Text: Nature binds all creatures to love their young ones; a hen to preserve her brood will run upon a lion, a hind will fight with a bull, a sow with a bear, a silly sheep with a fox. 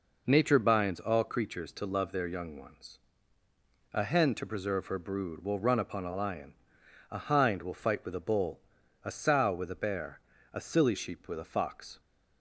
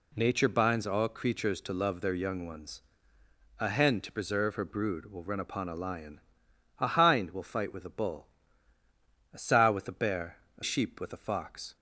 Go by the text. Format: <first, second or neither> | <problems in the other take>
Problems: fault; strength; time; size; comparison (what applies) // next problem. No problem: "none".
first | skips "silly"; at 10.6 s